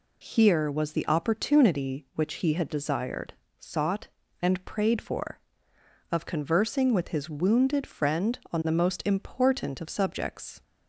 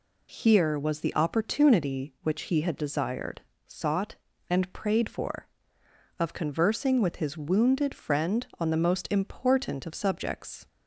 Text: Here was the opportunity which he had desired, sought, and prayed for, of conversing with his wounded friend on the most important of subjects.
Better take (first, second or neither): neither